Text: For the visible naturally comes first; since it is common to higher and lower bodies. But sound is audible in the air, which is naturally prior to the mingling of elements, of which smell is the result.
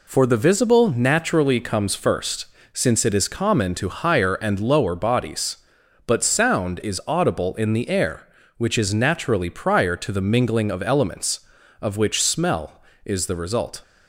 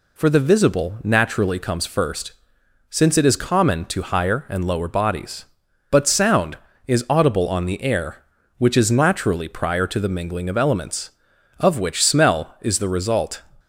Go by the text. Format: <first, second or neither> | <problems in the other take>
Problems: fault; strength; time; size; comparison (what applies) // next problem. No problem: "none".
first | says "on" for "in"; at 7.4 s